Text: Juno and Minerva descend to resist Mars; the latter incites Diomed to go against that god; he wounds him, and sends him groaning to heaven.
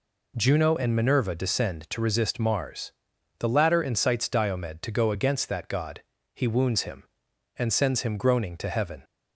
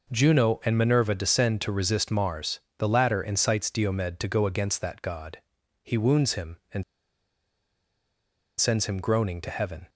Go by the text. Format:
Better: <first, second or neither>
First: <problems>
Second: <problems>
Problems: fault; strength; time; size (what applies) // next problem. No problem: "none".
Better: first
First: none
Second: pauses between "and" and "sends"; strong; at 6.8 s; 1.7 s long